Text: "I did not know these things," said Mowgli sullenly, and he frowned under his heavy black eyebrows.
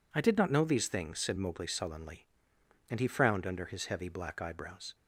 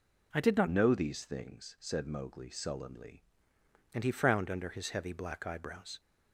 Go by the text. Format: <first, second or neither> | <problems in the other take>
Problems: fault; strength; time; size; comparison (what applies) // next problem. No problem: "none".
first | changes voice from "know" to "sullenly"; from 0.6 to 3.2 s; 2.6 s long